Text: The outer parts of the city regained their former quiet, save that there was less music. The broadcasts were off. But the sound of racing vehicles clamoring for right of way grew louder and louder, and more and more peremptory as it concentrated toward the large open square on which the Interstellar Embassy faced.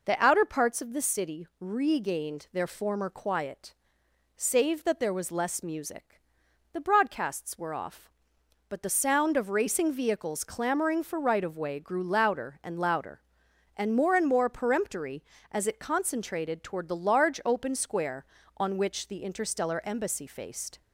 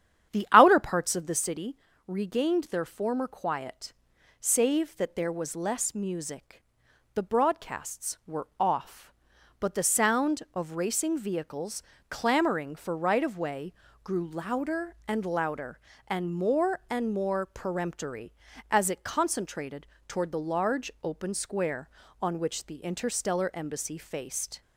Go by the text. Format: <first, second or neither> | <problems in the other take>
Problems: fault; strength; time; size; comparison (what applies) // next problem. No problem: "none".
first | starts louder than the rest; strong; until 1.7 s; 9.5 dB // pauses between "city" and "regained"; slight; at 1.7 s; 0.30 s long // pauses between "vehicles" and "clamoring"; slight; at 11.8 s; 0.30 s long // pauses between "way" and "grew"; slight; at 13.7 s; 0.30 s long // pauses between "concentrated" and "toward"; slight; at 19.8 s; 0.20 s long